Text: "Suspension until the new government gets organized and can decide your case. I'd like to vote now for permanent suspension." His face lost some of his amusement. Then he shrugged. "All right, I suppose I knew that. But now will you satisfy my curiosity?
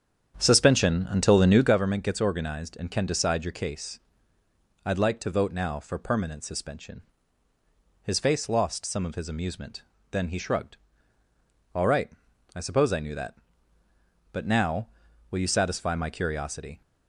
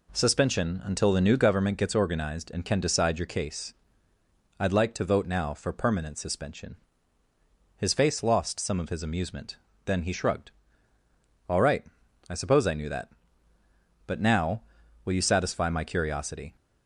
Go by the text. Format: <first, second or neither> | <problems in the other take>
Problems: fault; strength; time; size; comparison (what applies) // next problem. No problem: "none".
second | starts louder than the rest; strong; until 1.8 s; 8.5 dB